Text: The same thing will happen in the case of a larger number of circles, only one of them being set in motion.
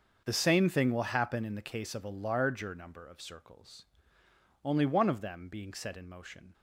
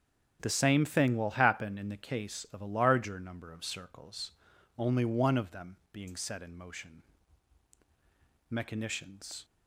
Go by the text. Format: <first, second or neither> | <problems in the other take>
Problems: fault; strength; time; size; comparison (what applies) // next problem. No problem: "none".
first | starts louder than the rest; strong; until 1.4 s; 7.5 dB; also in the first // pauses between "them" and "being"; slight; at 5.7 s; 0.16 s long // goes on to say "Mechanicians"; noticeable; from 8.4 s on; 0.96 s long